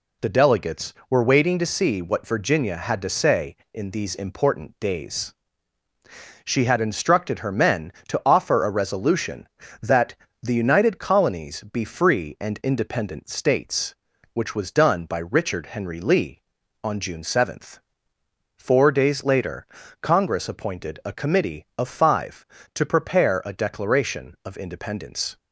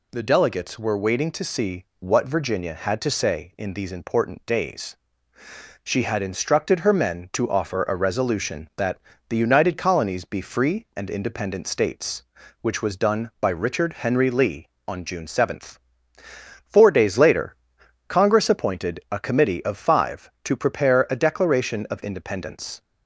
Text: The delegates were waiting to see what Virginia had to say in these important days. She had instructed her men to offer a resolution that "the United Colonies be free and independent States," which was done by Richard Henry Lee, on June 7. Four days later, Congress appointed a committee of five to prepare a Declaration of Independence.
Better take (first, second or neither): neither